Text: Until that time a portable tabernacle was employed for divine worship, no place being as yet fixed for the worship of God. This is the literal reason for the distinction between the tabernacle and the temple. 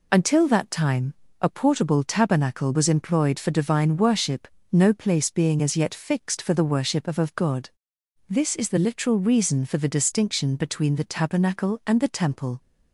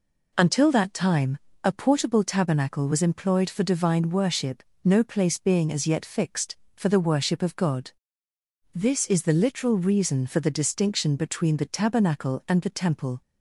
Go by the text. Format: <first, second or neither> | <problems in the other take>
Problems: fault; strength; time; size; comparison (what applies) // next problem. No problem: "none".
second | pauses between "time" and "a"; slight; at 1.1 s; 0.26 s long; slight in the second // says "of" twice; at 7.1 s